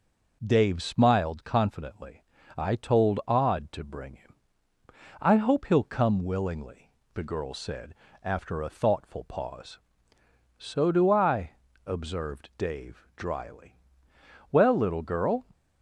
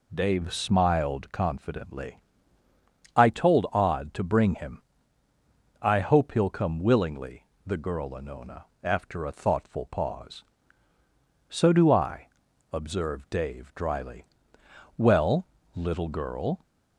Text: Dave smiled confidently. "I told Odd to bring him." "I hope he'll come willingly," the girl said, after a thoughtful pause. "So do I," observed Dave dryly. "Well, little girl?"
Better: first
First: none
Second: says "anona" for "said"; at 8.1 s

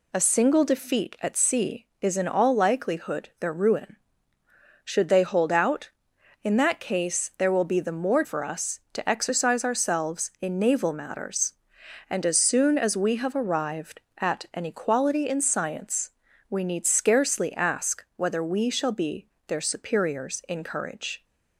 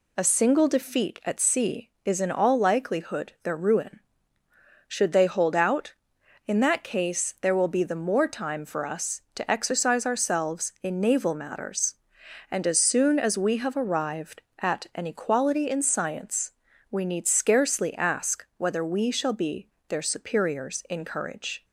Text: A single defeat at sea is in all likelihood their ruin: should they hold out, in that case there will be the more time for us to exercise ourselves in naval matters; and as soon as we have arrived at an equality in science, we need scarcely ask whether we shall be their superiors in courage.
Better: second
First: skips "time"; at 8.2 s // pauses between "be" and "their"; slight; at 19.2 s; 0.18 s long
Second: pauses between "be" and "their"; slight; at 19.6 s; 0.18 s long

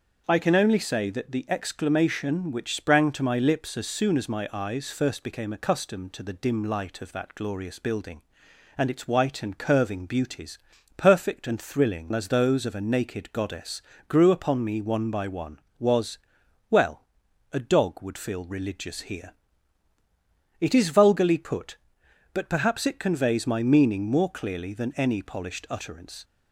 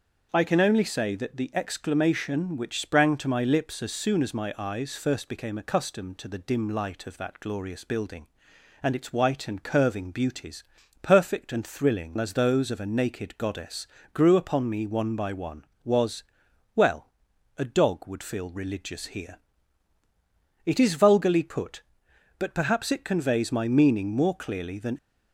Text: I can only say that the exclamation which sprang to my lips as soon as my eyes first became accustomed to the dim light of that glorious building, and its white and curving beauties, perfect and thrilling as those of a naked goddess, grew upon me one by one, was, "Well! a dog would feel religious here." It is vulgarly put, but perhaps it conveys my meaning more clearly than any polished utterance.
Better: first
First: starts louder than the rest; until 1.2 s; 6.5 dB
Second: starts louder than the rest; until 1.3 s; 6.5 dB // stops before "any polished utterance"; at 24.9 s

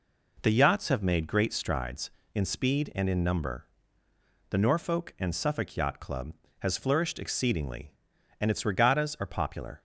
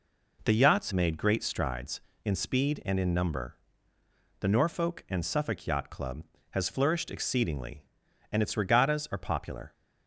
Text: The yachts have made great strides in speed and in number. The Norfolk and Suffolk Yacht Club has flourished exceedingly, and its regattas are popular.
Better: first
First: none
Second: skips "have"; at 0.9 s

